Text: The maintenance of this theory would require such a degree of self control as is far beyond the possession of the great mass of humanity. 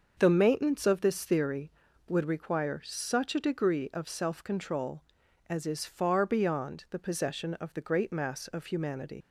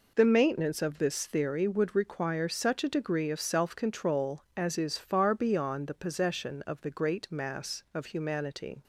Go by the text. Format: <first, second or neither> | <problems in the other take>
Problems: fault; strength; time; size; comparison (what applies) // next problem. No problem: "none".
second | starts louder than the rest; until 1.1 s; 6.5 dB // leaves "humanity" unfinished; at 9.2 s; 95 ms